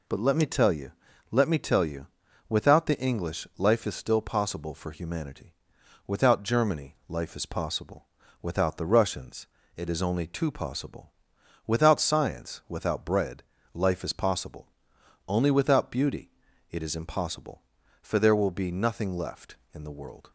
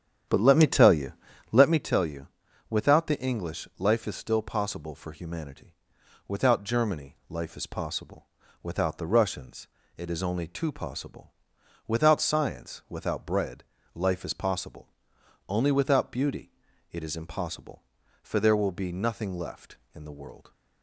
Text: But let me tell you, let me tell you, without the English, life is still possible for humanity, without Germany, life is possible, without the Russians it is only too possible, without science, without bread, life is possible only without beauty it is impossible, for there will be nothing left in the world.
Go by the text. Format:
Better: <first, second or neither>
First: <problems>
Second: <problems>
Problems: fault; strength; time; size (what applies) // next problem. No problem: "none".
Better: first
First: pauses between "Russians" and "it"; slight; at 9.4 s; 0.30 s long // pauses between "possible" and "only"; noticeable; at 14.6 s; 0.62 s long // pauses between "beauty" and "it"; at 16.3 s; 0.40 s long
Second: starts louder than the rest; strong; until 1.8 s; 9 dB // pauses between "Russians" and "it"; slight; at 9.6 s; 0.30 s long // pauses between "possible" and "only"; noticeable; at 14.8 s; 0.62 s long // pauses between "beauty" and "it"; at 16.5 s; 0.40 s long